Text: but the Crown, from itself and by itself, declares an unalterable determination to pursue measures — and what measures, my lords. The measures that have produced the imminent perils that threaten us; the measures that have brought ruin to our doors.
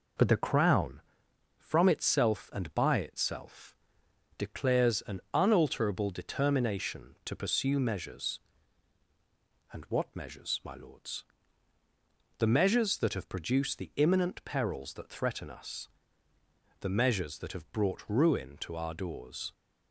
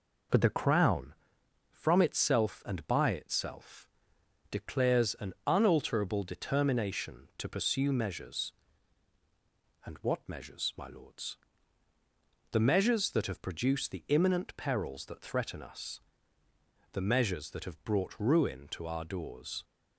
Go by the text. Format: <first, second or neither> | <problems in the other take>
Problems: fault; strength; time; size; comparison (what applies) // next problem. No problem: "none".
neither | none